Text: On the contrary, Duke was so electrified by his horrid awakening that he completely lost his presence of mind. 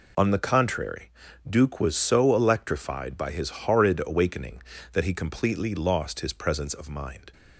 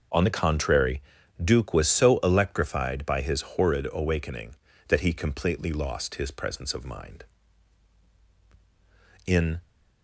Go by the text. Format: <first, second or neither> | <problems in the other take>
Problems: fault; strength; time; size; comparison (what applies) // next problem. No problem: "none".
first | goes on to say "In"; slight; from 9.2 s on; 0.36 s long